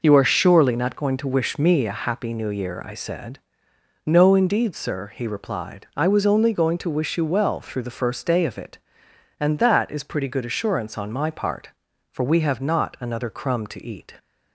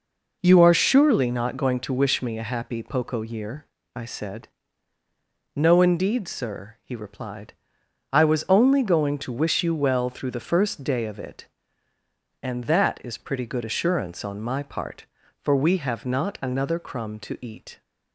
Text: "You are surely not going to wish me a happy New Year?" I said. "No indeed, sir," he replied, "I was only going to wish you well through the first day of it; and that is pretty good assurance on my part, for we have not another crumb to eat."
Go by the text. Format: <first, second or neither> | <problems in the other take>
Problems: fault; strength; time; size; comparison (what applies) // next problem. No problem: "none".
first | says "Poco" for "New"; at 2.8 s